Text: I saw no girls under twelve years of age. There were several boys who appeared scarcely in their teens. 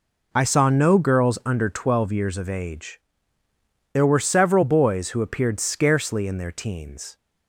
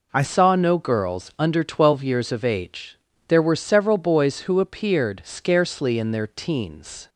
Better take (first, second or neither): first